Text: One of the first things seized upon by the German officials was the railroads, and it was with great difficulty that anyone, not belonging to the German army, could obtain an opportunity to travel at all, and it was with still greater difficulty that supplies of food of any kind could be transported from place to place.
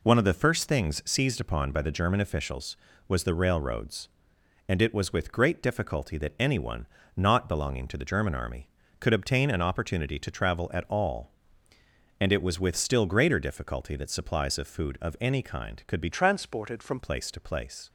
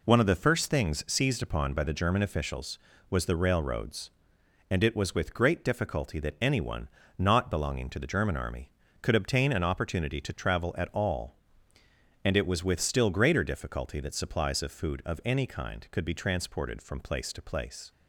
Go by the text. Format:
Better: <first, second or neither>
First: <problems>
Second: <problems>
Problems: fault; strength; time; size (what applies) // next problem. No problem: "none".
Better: second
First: changes voice from "transported" to "from"; from 16.1 to 16.9 s; 0.8 s long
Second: none